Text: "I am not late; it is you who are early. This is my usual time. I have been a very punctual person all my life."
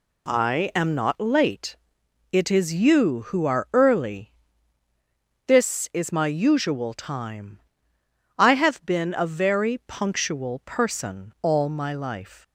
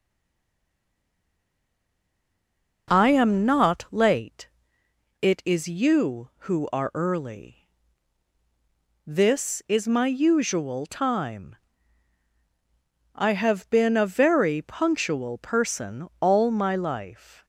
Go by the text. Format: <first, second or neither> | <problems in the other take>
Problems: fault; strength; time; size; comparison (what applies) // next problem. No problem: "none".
first | stays silent before the first word; strong; until 2.8 s; 2.8 s long